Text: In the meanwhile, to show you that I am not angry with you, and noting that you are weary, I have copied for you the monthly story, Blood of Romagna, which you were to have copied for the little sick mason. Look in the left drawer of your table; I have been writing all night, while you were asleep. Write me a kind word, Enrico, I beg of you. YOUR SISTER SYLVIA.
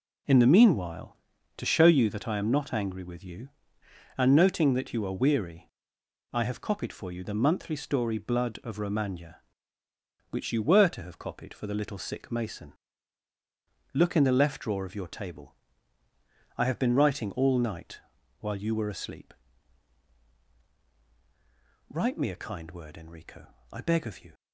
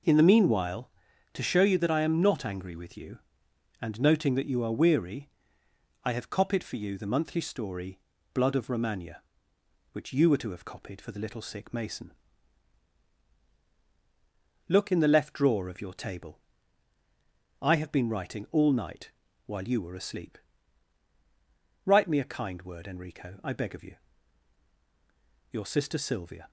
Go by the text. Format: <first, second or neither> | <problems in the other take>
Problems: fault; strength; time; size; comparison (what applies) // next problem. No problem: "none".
second | stops before "YOUR SISTER SYLVIA"; at 24.3 s